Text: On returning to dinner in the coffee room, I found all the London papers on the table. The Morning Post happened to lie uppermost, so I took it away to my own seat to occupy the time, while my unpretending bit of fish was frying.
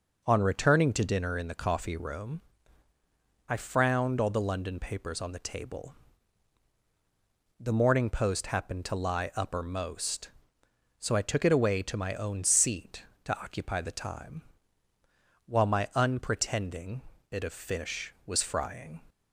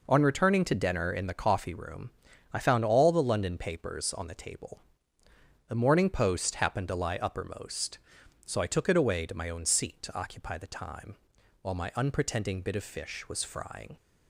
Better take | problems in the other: second | says "frowned" for "found"; at 3.5 s // pauses between "unpretending" and "bit"; slight; at 17.0 s; 0.28 s long

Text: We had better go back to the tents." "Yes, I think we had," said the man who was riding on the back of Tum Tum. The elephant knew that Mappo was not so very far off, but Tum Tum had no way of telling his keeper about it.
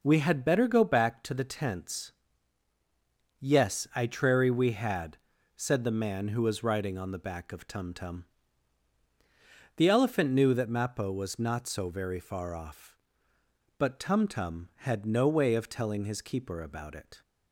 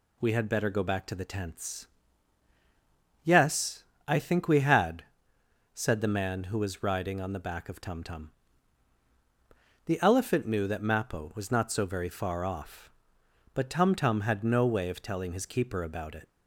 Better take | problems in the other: second | says "trary" for "think"; at 4.0 s

